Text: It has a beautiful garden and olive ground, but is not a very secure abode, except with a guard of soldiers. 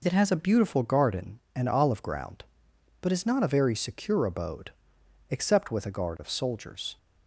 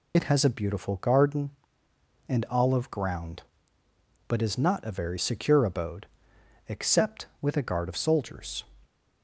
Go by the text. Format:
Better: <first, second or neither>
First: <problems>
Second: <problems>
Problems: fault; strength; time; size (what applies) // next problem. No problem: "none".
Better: first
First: none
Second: loses the start of "It"; at 0.1 s; 55 ms